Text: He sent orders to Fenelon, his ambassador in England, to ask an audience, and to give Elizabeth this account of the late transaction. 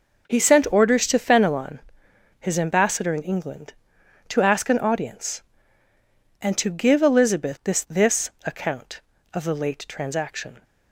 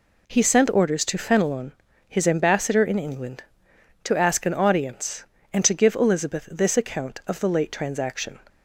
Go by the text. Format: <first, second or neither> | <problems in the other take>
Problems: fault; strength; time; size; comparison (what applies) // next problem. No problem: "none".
second | says "this" twice; at 7.8 s